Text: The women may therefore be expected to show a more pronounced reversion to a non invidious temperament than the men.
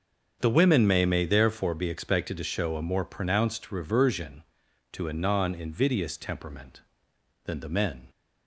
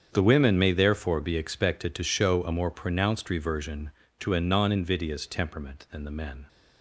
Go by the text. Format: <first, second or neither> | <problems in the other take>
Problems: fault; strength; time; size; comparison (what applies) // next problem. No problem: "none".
second | starts louder than the rest; until 1.4 s; 6.5 dB; strong in the second // says "may" twice; at 1.0 s